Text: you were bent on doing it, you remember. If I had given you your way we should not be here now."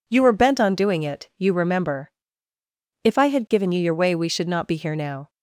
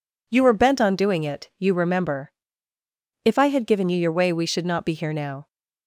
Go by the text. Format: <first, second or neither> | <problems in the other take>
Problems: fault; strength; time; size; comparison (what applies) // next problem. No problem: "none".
neither | none